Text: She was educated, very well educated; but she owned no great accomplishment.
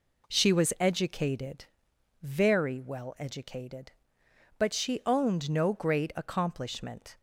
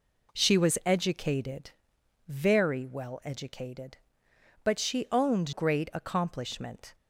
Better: first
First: none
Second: skips "no"; at 5.5 s

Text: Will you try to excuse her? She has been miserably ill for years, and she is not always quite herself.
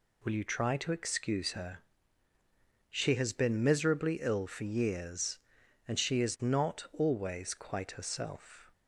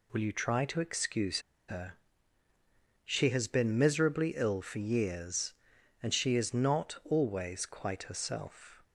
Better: first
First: none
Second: pauses between "excuse" and "her"; slight; at 1.4 s; 0.27 s long

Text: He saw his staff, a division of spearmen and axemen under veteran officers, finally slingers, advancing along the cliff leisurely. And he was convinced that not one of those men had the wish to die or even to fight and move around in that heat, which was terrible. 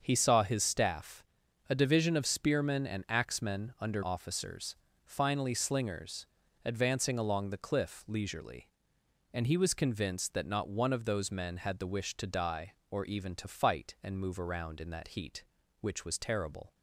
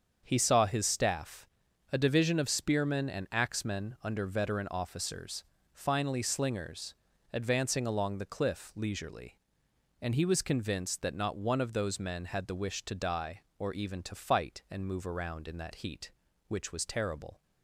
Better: second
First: starts louder than the rest; until 1.0 s; 7 dB // skips "veteran"; at 4.0 s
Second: starts louder than the rest; strong; until 1.2 s; 7 dB

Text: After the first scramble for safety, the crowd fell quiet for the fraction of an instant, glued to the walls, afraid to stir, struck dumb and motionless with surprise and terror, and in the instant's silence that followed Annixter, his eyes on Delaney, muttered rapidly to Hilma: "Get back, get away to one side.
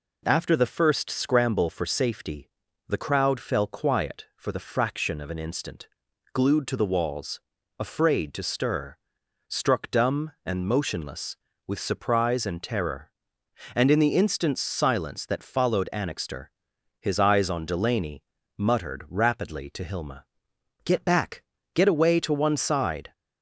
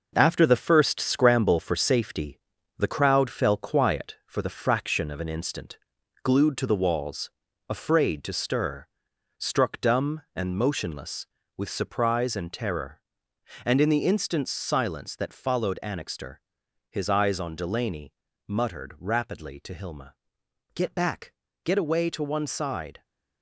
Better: first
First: none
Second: gets quieter; throughout; 7 dB

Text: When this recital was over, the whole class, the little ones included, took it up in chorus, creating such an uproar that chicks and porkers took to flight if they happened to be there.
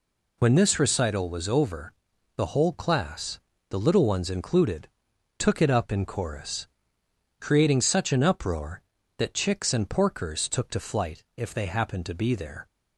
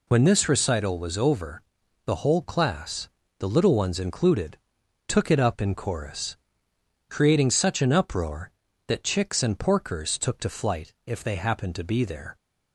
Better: neither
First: pauses between "flight" and "if"; slight; at 11.2 s; 0.16 s long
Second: pauses between "flight" and "if"; slight; at 10.9 s; 0.16 s long

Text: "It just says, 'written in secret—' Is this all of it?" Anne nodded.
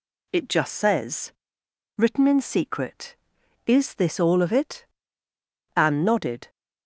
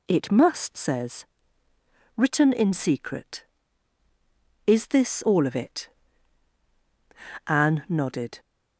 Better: first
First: none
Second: says "must" for "just"; at 0.2 s

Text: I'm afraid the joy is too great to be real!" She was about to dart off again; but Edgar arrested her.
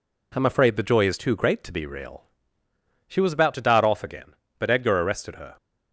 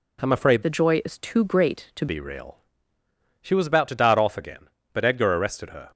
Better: first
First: none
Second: changes voice from "the" to "to"; from 0.6 to 2.0 s; 1.4 s long

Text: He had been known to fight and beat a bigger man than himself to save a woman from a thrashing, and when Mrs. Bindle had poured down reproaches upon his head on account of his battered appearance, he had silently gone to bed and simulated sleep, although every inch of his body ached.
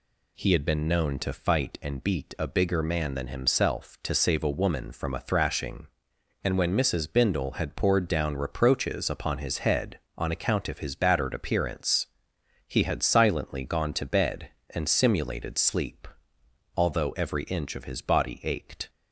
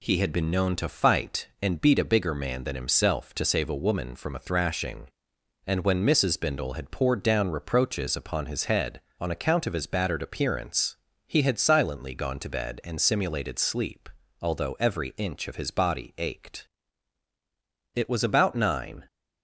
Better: first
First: none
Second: goes on to say "It was about nine"; noticeable; from 17.9 s on; 1.1 s long

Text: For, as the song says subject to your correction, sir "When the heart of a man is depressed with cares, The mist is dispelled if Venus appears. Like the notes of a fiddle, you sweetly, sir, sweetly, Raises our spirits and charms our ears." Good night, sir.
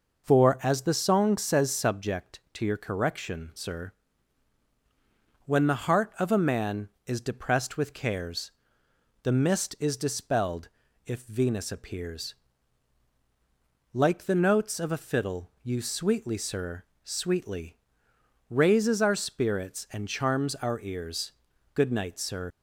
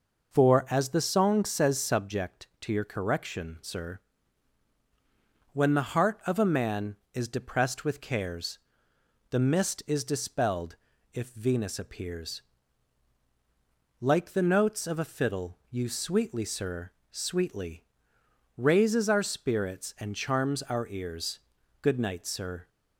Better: second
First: pauses between "sir" and "When"; strong; at 3.9 s; 1.5 s long // pauses between "dispelled" and "if"; slight; at 10.6 s; 0.36 s long // leaves "sir" unfinished; at 22.5 s; 105 ms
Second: pauses between "sir" and "When"; strong; at 4.0 s; 1.5 s long // pauses between "dispelled" and "if"; slight; at 10.7 s; 0.36 s long

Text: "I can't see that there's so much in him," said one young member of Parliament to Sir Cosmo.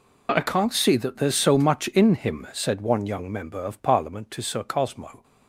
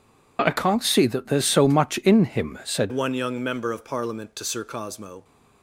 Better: first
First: none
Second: changes voice at "one"; from 2.9 s on; 2.3 s long

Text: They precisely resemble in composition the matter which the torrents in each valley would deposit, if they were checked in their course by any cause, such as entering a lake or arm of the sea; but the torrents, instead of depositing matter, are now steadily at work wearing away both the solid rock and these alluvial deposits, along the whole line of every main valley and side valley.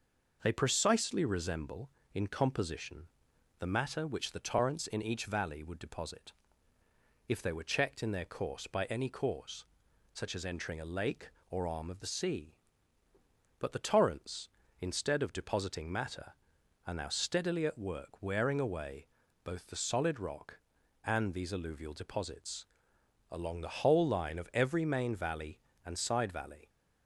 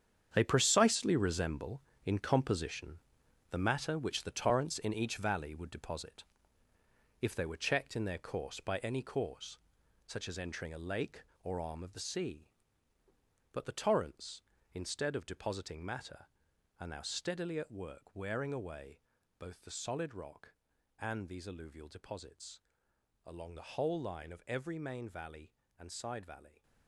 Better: first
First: pauses between "composition" and "the"; noticeable; at 3.0 s; 0.52 s long // pauses between "away" and "both"; at 19.0 s; 0.37 s long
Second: gets quieter; strong; throughout; 12 dB // pauses between "composition" and "the"; noticeable; at 2.9 s; 0.52 s long // pauses between "away" and "both"; slight; at 19.0 s; 0.36 s long

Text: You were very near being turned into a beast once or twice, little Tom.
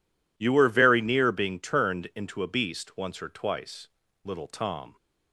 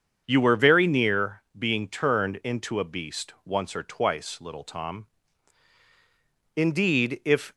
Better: first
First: none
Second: starts louder than the rest; until 1.2 s; 7 dB // pauses between "near" and "being"; slight; at 1.4 s; 0.16 s long // goes on to say "Indeed if"; noticeable; from 6.5 s on; 0.98 s long

